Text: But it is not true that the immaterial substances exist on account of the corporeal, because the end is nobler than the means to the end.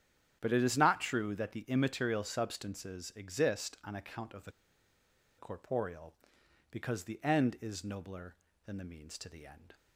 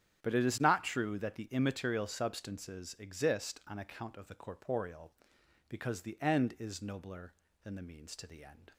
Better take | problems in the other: second | starts louder than the rest; strong; until 1.4 s; 10 dB; strong in the second // pauses between "the" and "corporeal"; noticeable; at 4.5 s; 0.87 s long

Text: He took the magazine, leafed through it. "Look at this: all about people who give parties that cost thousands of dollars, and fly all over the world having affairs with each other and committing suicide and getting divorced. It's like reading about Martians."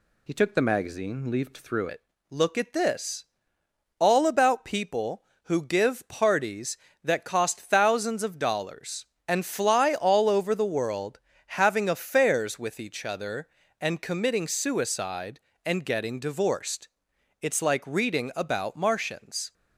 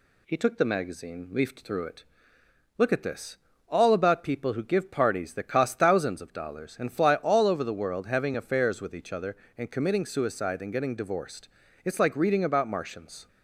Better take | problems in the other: second | changes voice at "it"; from 1.8 s on; 17.7 s long // pauses between "world" and "having"; slight; at 11.2 s; 0.36 s long

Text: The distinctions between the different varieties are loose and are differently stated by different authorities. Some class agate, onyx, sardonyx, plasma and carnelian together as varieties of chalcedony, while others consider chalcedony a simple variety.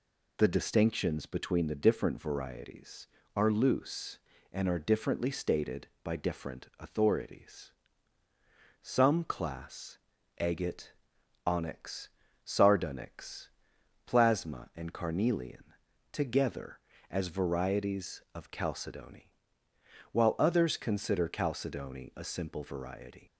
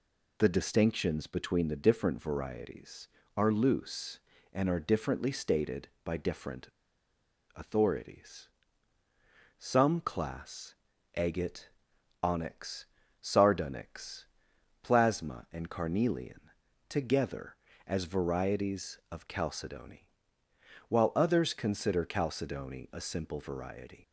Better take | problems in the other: first | pauses between "different" and "authorities"; noticeable; at 6.6 s; 0.87 s long // pauses between "class" and "agate"; at 10.7 s; 0.42 s long; also in the first // pauses between "carnelian" and "together"; noticeable; at 16.4 s; 0.48 s long; noticeable in the first

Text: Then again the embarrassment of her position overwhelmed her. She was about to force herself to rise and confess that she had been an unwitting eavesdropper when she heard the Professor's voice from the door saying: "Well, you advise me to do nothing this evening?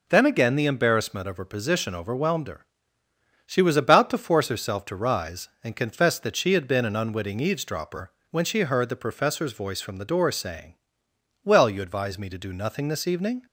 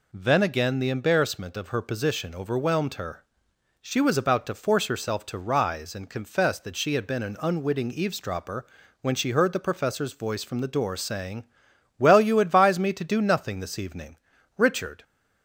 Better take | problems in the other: first | pauses between "eavesdropper" and "when"; slight; at 8.6 s; 0.36 s long; slight in the first // goes on to say "Richard"; slight; from 14.5 s on; 0.46 s long

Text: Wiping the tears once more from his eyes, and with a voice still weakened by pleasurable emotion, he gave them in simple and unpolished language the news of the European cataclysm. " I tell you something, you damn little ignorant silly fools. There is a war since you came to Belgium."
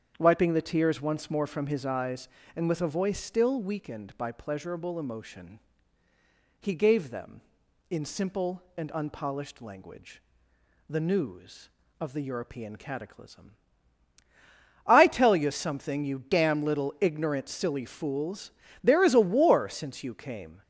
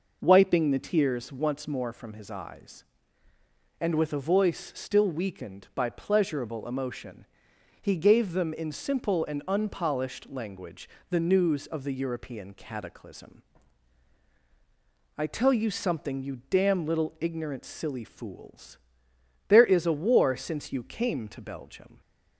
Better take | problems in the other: second | starts louder than the rest; strong; until 1.1 s; 8 dB // pauses between "language" and "the"; noticeable; at 10.2 s; 0.66 s long; slight in the second // stops before "to Belgium"; at 20.6 s

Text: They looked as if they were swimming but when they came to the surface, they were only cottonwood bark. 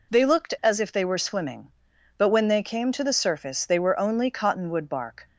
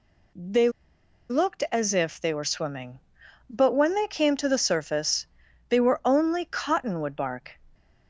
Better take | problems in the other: first | pauses between "They" and "looked"; noticeable; at 0.6 s; 0.60 s long

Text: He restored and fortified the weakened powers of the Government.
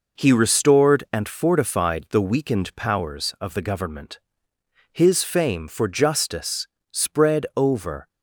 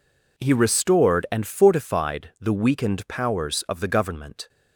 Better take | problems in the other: second | goes on to say "His fame for justice spread over"; strong; from 4.9 s on; 3.1 s long

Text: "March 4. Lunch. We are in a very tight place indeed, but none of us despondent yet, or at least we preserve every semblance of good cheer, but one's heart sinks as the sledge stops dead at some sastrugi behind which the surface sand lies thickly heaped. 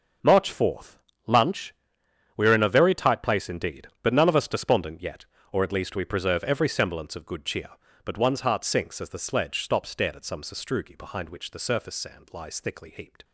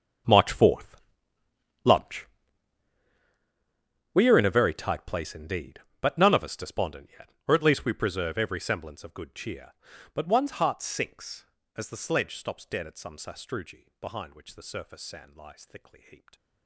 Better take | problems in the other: first | gets quieter; strong; throughout; 18.5 dB // starts louder than the rest; strong; until 2.1 s; 7.5 dB; also in the first

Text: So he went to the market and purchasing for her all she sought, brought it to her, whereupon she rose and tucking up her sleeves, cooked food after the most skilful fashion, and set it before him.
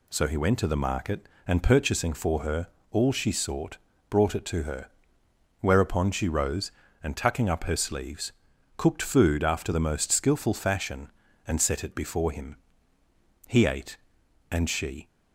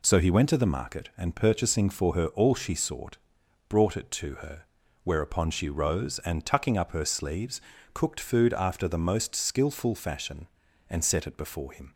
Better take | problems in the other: second | pauses between "her" and "all"; slight; at 2.6 s; 0.24 s long // goes on to say "He ate and she"; from 13.4 s on; 1.6 s long

